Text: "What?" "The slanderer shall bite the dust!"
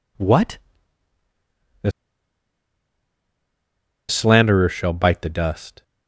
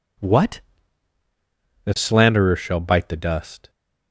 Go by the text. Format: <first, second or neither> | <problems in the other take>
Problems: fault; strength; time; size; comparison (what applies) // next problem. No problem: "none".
second | pauses between "The" and "slanderer"; strong; at 1.8 s; 2.1 s long